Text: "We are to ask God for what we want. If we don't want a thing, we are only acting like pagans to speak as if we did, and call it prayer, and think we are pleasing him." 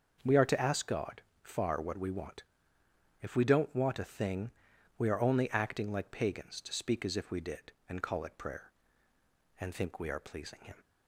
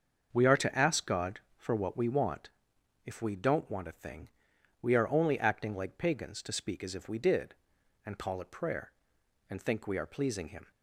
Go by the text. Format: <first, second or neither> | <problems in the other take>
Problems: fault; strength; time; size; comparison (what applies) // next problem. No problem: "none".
second | starts louder than the rest; until 1.4 s; 6.5 dB; also in the second // says "far" for "for"; at 1.4 s